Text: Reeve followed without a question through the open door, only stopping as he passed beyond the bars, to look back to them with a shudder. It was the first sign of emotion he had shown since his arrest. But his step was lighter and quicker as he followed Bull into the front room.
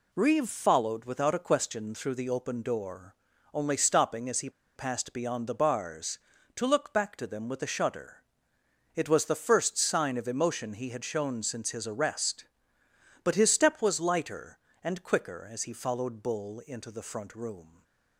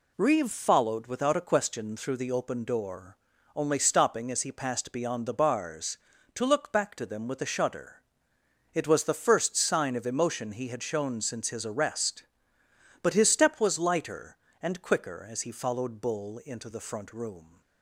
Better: second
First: pauses between "he" and "passed"; slight; at 4.4 s; 0.25 s long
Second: none

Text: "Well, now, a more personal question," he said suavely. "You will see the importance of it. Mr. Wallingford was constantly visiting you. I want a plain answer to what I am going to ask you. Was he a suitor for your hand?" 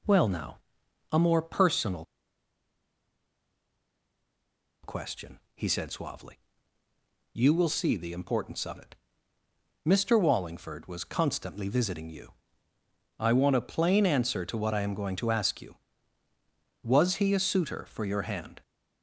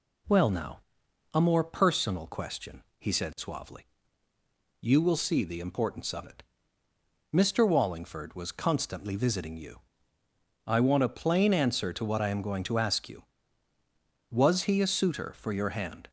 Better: second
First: pauses between "personal" and "question"; strong; at 2.0 s; 2.7 s long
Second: none

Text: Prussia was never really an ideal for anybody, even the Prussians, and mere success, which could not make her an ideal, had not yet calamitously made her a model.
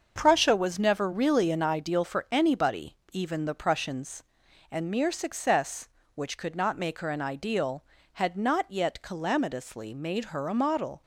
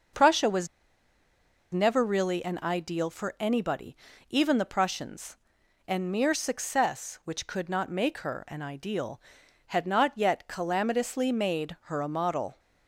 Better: first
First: starts louder than the rest; until 1.1 s; 6.5 dB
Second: starts louder than the rest; until 2.2 s; 6 dB // pauses between "was" and "never"; at 0.6 s; 1.0 s long

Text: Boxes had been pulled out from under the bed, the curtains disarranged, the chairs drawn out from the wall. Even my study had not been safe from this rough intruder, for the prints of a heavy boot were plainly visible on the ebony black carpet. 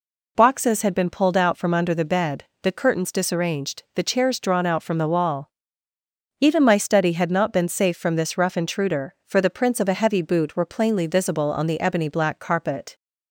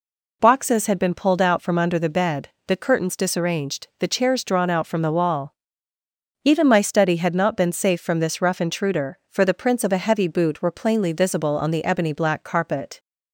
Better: neither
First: none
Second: none

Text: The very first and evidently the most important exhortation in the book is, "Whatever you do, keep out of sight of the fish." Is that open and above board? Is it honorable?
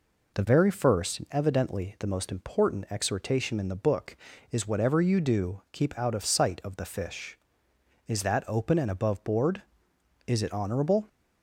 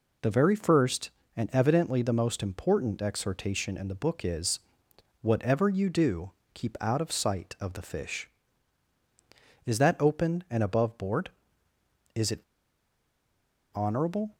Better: first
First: none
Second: pauses between "it" and "honorable"; strong; at 12.4 s; 1.3 s long

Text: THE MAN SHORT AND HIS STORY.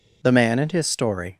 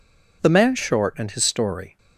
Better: second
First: skips "SHORT"; at 0.5 s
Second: none

